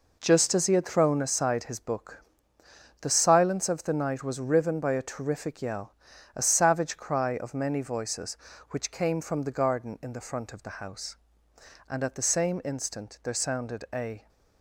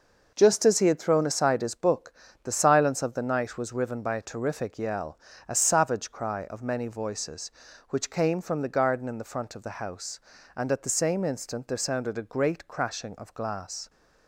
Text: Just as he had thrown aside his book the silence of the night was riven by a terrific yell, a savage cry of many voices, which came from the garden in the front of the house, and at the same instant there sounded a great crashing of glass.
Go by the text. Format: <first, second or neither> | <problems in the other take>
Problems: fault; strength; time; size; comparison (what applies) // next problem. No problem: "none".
second | pauses between "book" and "the"; noticeable; at 2.2 s; 0.78 s long; slight in the second // stops before "great crashing of glass"; at 14.2 s